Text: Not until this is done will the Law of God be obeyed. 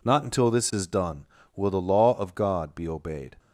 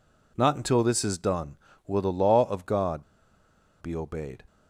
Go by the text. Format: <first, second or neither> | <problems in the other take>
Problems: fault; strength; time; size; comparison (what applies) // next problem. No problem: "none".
first | pauses between "God" and "be"; noticeable; at 3.0 s; 0.78 s long